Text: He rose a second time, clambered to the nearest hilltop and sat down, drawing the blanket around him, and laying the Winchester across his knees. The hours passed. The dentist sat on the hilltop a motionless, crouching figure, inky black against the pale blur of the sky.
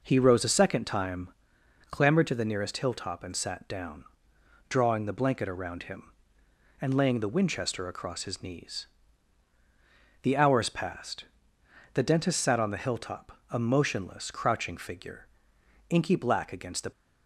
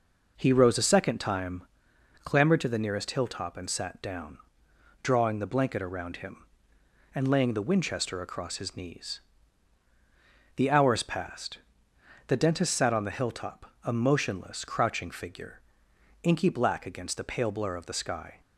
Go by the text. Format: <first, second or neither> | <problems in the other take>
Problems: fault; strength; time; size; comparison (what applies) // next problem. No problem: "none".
second | stops before "pale blur of the sky"; at 16.9 s